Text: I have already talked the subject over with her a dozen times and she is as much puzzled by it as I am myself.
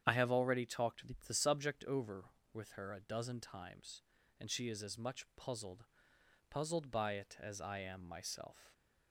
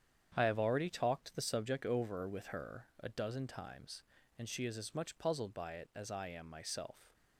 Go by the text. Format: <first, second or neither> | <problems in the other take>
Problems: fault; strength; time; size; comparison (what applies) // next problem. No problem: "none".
second | starts louder than the rest; strong; until 1.2 s; 9 dB; strong in the second // pauses between "talked" and "the"; slight; at 1.0 s; 0.22 s long // says "puzzled" twice; at 6.4 s